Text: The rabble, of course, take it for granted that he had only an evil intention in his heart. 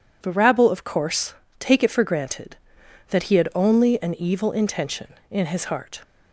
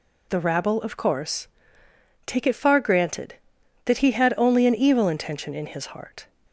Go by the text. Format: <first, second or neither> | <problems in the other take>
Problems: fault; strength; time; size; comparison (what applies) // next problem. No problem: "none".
first | says "far" for "for"; at 2.5 s